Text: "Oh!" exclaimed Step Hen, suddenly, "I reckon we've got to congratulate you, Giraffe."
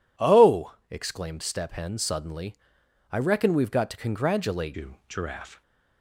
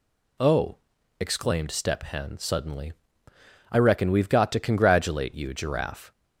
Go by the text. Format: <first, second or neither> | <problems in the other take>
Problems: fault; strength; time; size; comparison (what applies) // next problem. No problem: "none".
second | changes voice at "you"; from 4.7 s on; 0.9 s long